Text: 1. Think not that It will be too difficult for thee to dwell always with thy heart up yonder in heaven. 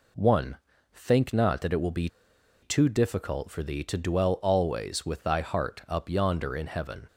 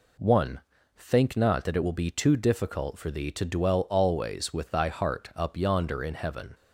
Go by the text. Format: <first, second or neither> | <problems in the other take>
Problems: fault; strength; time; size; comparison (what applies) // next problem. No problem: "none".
second | pauses between "be" and "too"; noticeable; at 2.0 s; 0.55 s long